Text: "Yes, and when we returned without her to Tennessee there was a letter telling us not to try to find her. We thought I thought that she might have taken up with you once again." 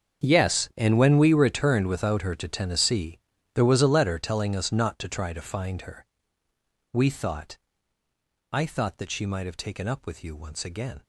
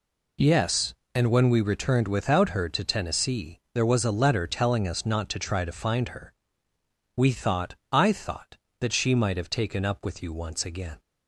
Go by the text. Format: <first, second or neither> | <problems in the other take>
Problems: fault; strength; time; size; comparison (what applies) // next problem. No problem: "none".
second | gets quieter; strong; throughout; 17 dB // pauses between "Tennessee" and "there"; slight; at 3.1 s; 0.36 s long // pauses between "thought" and "I"; noticeable; at 7.5 s; 0.96 s long; slight in the second